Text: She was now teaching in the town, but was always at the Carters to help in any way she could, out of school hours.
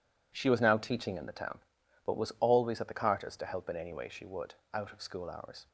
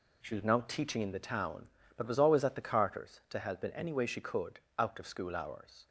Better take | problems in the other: second | says "would" for "could"; at 4.2 s

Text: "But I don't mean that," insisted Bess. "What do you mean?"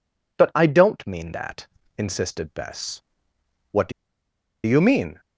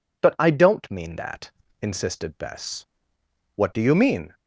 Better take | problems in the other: second | pauses between "do" and "you"; noticeable; at 3.9 s; 0.73 s long

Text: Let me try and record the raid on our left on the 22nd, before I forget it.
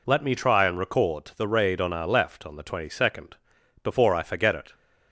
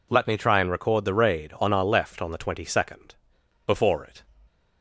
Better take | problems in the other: first | skips "I forget"; at 4.0 s

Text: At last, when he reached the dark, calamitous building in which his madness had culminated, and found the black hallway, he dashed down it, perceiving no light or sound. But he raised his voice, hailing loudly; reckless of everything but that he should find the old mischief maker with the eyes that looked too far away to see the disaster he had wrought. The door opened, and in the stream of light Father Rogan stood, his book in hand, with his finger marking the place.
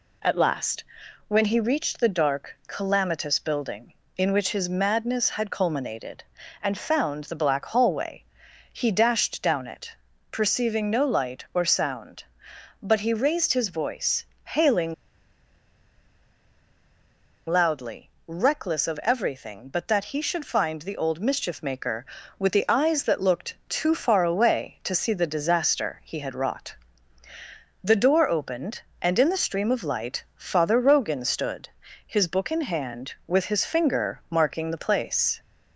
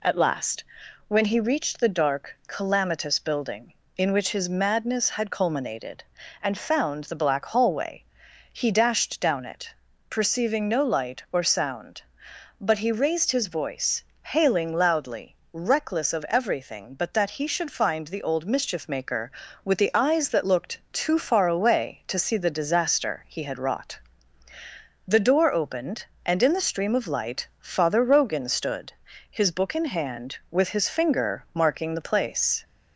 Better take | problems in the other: second | pauses between "hailing" and "loudly"; strong; at 14.9 s; 2.5 s long

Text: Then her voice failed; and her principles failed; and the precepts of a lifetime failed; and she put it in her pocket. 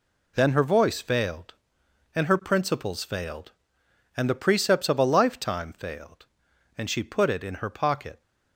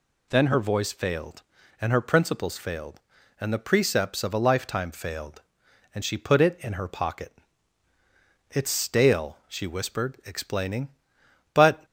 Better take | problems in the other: first | goes on to say "It's stale she whispered explaining But"; strong; from 8.4 s on; 3.3 s long

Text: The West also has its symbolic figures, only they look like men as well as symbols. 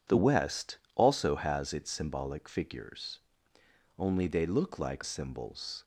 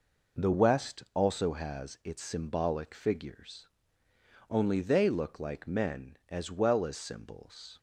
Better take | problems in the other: second | pauses between "West" and "also"; slight; at 0.7 s; 0.18 s long // skips "men as well as"; at 5.0 s

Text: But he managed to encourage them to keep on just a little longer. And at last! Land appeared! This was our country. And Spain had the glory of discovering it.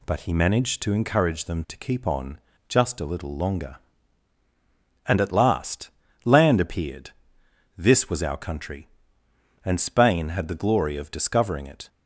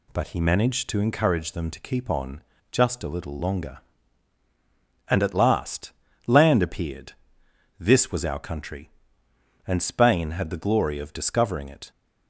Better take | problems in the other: neither | pauses between "on" and "just"; slight; the same in both

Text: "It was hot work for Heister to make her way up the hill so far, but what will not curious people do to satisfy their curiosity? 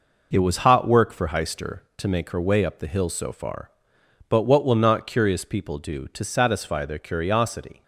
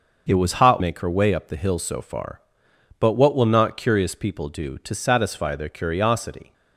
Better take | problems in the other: first | starts louder than the rest; until 1.2 s; 6 dB // skips "work for Heister to"; at 0.8 s

